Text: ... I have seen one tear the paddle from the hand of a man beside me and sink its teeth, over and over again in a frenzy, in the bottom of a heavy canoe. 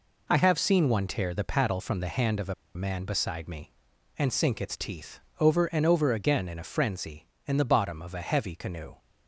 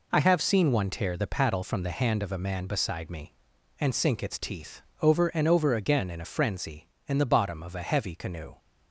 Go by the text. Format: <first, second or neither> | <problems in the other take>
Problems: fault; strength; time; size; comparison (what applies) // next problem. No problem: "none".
second | pauses between "a" and "man"; slight; at 2.5 s; 0.22 s long